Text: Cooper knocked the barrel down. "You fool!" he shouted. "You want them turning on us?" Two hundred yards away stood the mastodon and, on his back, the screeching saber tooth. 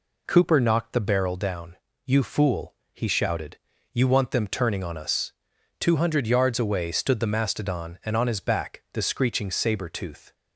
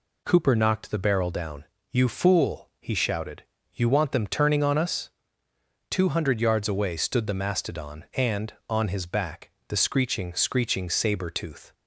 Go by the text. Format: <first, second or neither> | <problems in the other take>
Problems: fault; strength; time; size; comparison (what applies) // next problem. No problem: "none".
first | says "screeching" twice; at 10.3 s